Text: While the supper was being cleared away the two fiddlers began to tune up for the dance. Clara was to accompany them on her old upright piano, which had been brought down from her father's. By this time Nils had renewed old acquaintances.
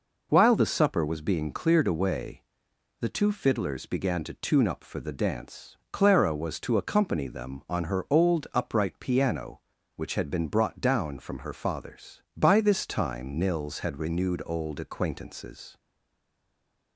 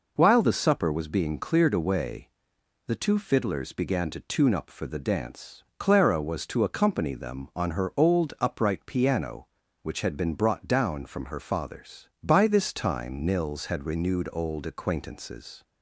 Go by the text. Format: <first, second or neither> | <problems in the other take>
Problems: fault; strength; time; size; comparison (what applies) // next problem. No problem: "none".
second | pauses between "away" and "the"; noticeable; at 2.4 s; 0.58 s long; noticeable in the second // stays silent after the last word; noticeable; from 15.7 s on; 1.2 s long